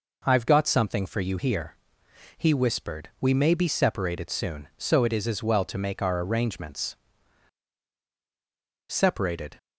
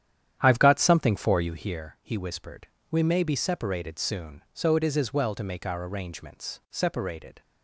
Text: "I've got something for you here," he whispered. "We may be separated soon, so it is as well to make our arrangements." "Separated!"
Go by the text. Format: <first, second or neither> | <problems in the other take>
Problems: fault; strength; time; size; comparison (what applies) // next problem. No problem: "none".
first | starts louder than the rest; strong; until 1.6 s; 10 dB